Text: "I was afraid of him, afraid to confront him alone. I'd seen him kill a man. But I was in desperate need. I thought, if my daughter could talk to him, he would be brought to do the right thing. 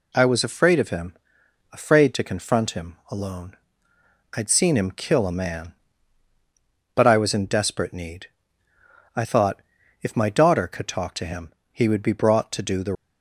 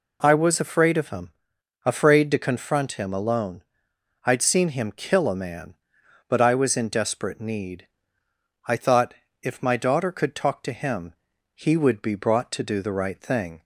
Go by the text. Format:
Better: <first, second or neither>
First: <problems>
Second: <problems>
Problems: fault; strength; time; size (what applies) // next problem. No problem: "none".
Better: second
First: stops before "right thing"; at 12.9 s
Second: none